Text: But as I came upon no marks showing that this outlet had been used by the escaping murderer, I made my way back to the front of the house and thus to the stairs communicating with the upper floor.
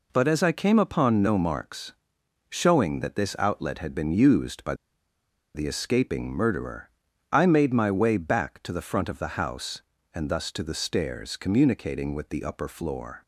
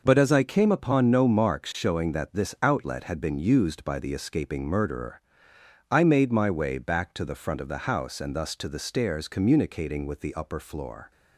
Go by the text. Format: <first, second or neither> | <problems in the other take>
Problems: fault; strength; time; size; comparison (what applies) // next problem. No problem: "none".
second | pauses between "marks" and "showing"; noticeable; at 1.9 s; 0.60 s long // pauses between "by" and "the"; noticeable; at 4.7 s; 0.80 s long